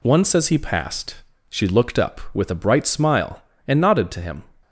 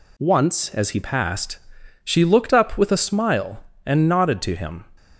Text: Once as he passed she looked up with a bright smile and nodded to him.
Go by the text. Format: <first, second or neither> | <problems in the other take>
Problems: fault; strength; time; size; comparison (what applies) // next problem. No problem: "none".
first | pauses between "passed" and "she"; noticeable; at 1.5 s; 0.48 s long; slight in the first // skips "bright"; at 2.9 s